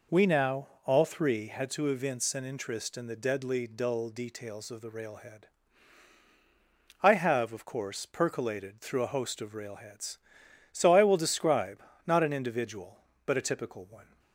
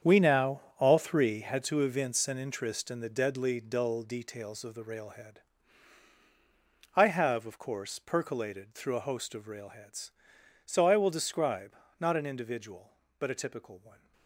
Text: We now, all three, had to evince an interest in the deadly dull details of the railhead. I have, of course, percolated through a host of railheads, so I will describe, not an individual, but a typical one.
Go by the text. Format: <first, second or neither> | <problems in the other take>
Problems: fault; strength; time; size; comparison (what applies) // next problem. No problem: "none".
first | gets quieter; strong; throughout; 12.5 dB